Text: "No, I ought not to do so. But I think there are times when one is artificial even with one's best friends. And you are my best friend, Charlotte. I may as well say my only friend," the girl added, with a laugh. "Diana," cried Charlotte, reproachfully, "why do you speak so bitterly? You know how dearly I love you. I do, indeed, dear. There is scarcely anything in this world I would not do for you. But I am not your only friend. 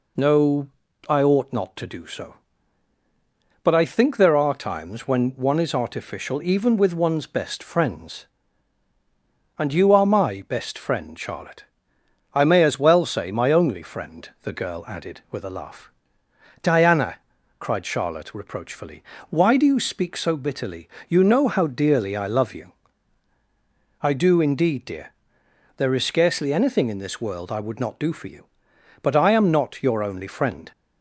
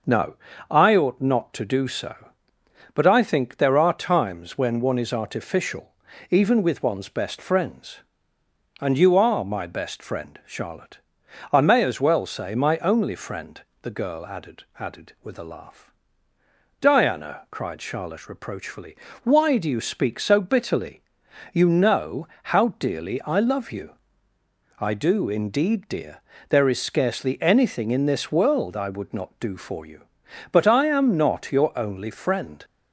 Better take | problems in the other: first | starts louder than the rest; until 1.4 s; 6.5 dB // pauses between "artificial" and "even"; at 5.8 s; 0.40 s long // says "added" twice; at 14.7 s // pauses between "know" and "how"; slight; at 22.2 s; 0.16 s long

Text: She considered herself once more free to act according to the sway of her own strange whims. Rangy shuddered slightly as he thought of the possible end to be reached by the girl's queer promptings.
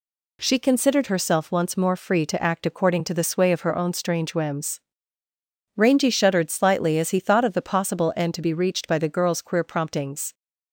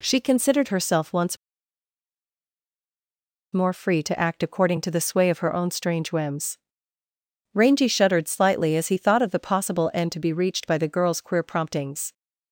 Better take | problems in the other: first | pauses between "once" and "more"; strong; at 1.3 s; 2.1 s long

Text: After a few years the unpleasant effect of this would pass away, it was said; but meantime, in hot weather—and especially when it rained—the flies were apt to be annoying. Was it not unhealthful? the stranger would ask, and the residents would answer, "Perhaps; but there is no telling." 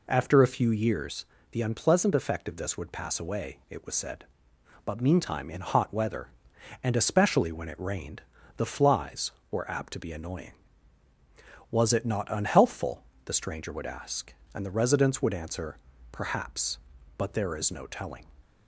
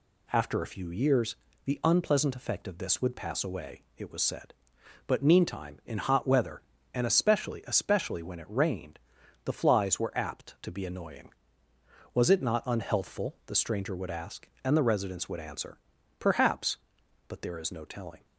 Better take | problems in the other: first | pauses between "years" and "the"; slight; at 1.3 s; 0.28 s long; slight in the first // says "especially" twice; at 7.6 s

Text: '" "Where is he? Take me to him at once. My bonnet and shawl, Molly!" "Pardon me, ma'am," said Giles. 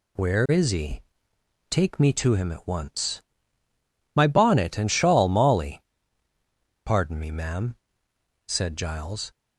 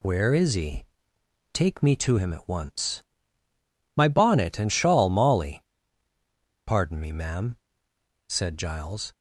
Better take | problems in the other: neither | none

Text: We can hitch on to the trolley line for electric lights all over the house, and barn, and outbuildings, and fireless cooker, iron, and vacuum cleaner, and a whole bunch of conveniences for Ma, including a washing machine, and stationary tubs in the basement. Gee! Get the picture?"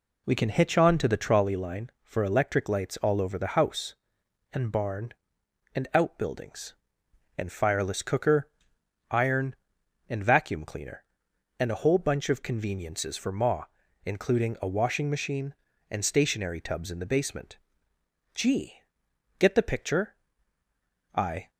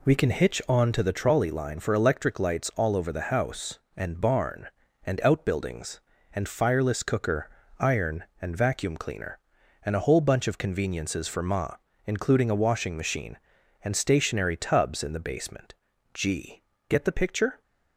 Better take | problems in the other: second | goes on to say "I"; slight; from 21.1 s on; 0.36 s long

